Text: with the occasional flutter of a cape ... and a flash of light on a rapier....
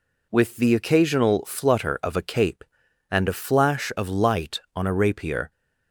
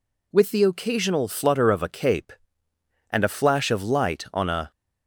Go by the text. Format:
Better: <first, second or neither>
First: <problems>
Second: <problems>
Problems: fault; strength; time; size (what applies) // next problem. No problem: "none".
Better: first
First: none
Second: stops before "rapier"; at 4.7 s